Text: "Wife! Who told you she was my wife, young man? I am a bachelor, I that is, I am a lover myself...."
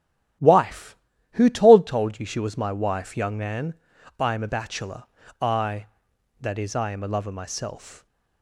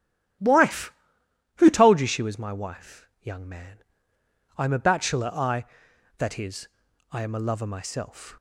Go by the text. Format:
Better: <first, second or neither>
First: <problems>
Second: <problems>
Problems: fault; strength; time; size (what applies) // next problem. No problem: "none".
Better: second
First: starts louder than the rest; strong; until 1.7 s; 11.5 dB // says "told" twice; at 1.8 s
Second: starts louder than the rest; strong; until 2.0 s; 12 dB